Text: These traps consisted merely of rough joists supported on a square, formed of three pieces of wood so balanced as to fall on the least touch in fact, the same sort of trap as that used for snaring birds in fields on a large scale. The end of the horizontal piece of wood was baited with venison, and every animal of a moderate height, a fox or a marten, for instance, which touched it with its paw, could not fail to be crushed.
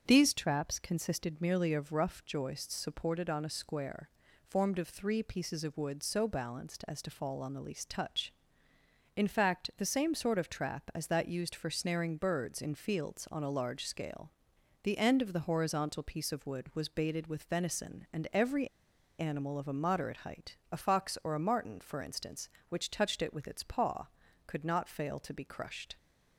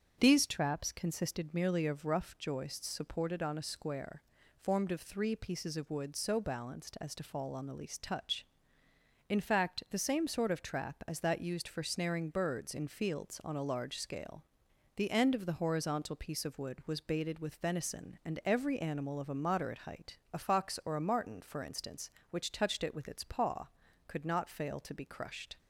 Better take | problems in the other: second | starts louder than the rest; strong; until 1.0 s; 7 dB; strong in the second // pauses between "every" and "animal"; noticeable; at 18.6 s; 0.52 s long

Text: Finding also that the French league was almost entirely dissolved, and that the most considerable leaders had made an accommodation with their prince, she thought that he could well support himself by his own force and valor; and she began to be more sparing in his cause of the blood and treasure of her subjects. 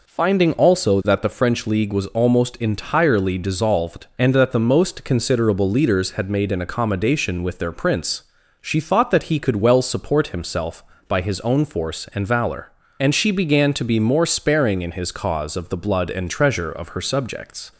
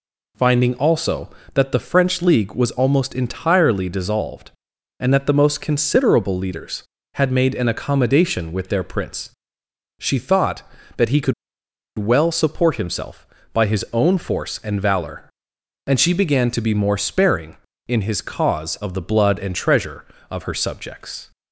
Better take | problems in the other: first | pauses between "could" and "well"; noticeable; at 11.3 s; 0.65 s long

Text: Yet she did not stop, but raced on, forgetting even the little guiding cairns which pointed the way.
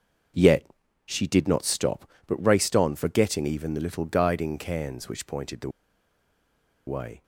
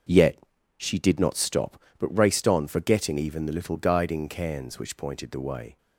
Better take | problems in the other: second | starts louder than the rest; until 1.7 s; 6.5 dB; also in the second // pauses between "Yet" and "she"; at 0.6 s; 0.38 s long; also in the second // pauses between "the" and "way"; at 5.6 s; 1.1 s long

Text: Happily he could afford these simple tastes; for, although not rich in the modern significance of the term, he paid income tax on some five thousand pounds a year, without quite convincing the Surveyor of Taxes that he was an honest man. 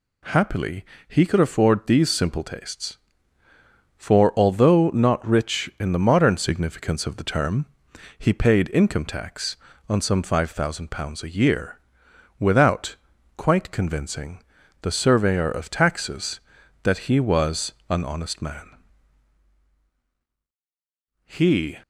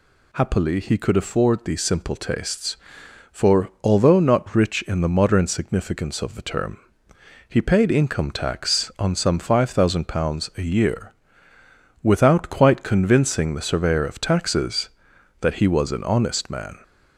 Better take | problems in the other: second | pauses between "Happily" and "he"; slight; at 0.8 s; 0.24 s long // pauses between "without" and "quite"; at 12.9 s; 0.40 s long // pauses between "convincing" and "the"; at 14.4 s; 0.38 s long // pauses between "was" and "an"; slight; at 17.7 s; 0.16 s long // goes on to say "He"; from 21.2 s on; 0.52 s long

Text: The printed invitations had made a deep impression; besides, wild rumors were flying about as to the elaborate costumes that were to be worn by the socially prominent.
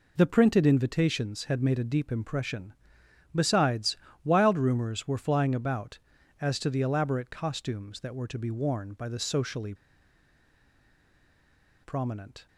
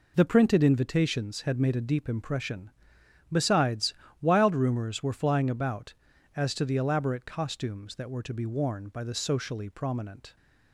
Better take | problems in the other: second | pauses between "socially" and "prominent"; strong; at 9.7 s; 2.0 s long

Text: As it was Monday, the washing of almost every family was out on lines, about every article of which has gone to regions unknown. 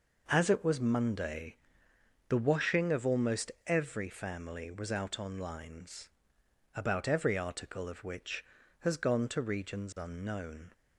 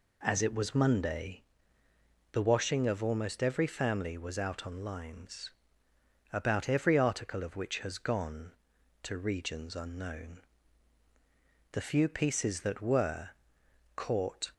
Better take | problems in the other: first | goes on to say "The few pieces that were Caught"; strong; from 11.7 s on; 2.8 s long

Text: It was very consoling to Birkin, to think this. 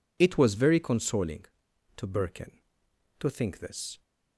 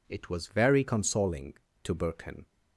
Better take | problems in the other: first | stops before "to think this"; at 2.4 s

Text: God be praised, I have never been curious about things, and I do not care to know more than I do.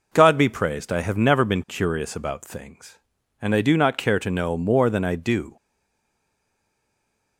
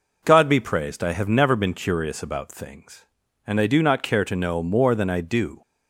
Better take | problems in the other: second | stays silent after the last word; noticeable; from 5.5 s on; 1.8 s long

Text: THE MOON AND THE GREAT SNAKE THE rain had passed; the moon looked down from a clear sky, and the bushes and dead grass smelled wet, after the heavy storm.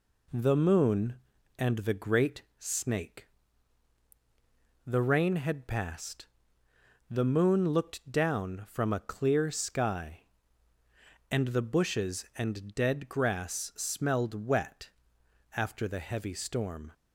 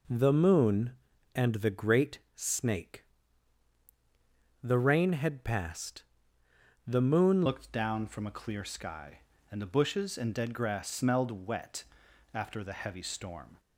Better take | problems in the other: first | pauses between "GREAT" and "SNAKE"; slight; at 2.1 s; 0.16 s long; slight in the first // pauses between "SNAKE" and "THE"; strong; at 3.0 s; 1.5 s long; strong in the first // changes voice at "looked"; from 7.4 s on; 6.1 s long

